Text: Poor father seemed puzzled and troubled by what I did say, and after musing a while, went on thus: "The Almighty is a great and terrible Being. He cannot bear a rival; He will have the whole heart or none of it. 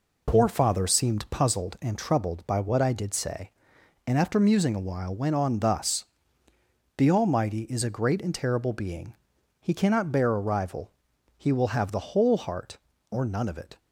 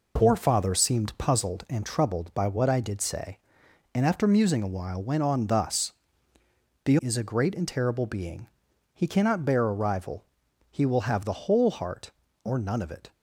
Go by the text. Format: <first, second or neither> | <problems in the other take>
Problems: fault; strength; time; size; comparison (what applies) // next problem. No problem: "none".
first | skips "Almighty"; at 6.9 s